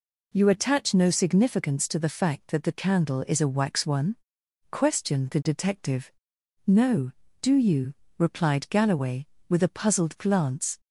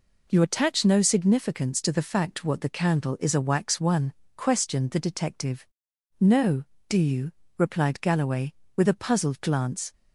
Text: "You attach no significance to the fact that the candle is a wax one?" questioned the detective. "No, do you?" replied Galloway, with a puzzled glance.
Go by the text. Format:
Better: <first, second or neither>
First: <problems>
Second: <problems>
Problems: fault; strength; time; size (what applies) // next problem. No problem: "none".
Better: first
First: none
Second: says "what" for "that"; at 2.4 s